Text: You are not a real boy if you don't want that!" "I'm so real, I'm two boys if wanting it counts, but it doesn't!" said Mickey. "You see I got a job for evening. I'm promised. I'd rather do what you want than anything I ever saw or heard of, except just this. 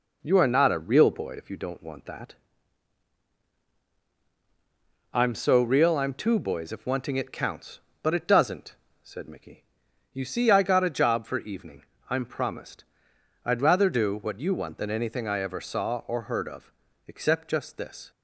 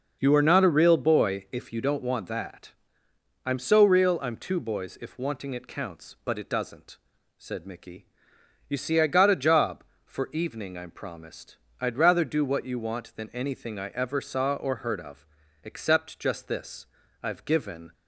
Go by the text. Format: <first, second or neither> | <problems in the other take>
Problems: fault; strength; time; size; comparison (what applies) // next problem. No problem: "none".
first | goes on to say "I've given"; noticeable; from 17.2 s on; 0.70 s long